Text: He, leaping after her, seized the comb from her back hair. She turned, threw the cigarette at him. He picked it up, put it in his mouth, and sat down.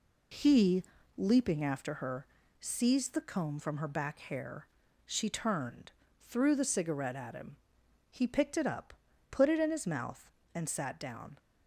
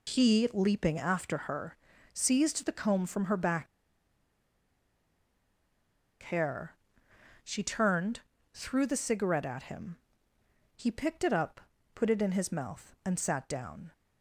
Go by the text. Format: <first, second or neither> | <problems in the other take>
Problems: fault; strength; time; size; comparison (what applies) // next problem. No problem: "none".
first | pauses between "back" and "hair"; strong; at 3.6 s; 2.5 s long